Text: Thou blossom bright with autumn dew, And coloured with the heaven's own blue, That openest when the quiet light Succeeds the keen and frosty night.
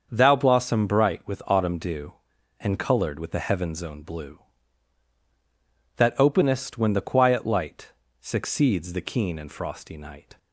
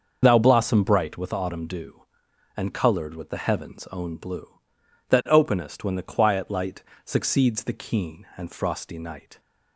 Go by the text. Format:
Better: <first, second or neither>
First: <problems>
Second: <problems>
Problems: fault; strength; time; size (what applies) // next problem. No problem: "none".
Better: first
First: starts louder than the rest; until 1.1 s; 6.5 dB // pauses between "light" and "Succeeds"; slight; at 7.9 s; 0.30 s long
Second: loses the start of "Thou"; at 0.2 s; 40 ms // starts louder than the rest; until 1.2 s; 6.5 dB // pauses between "light" and "Succeeds"; slight; at 6.8 s; 0.22 s long